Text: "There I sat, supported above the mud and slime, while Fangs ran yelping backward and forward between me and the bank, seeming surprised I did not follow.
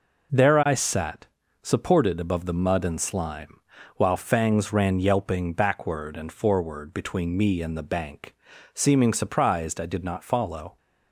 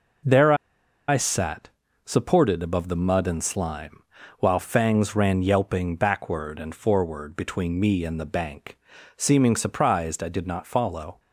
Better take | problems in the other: first | pauses between "There" and "I"; noticeable; at 0.5 s; 0.54 s long

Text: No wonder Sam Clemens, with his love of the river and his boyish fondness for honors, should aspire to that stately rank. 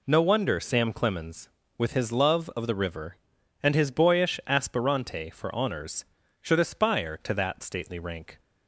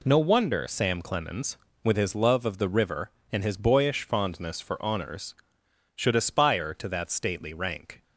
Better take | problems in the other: second | says "aspirante" for "fondness"; at 4.4 s

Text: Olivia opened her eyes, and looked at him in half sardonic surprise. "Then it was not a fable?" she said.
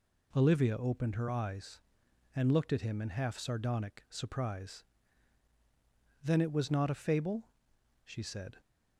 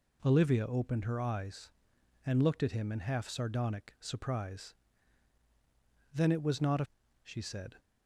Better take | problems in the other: first | skips "fable"; at 7.0 s

